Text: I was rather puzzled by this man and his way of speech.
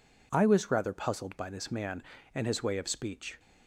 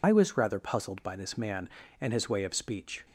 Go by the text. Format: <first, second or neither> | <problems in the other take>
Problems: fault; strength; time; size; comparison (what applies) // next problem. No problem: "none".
first | loses the start of "I"; at 0.0 s; 65 ms